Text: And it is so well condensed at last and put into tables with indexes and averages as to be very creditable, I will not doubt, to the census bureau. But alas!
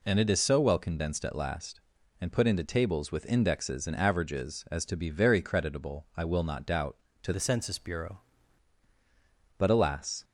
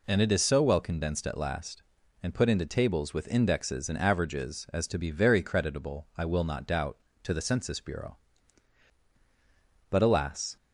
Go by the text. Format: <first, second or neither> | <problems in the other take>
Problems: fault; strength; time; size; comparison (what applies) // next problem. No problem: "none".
second | changes voice from "the" to "bureau"; from 7.3 to 8.1 s; 0.8 s long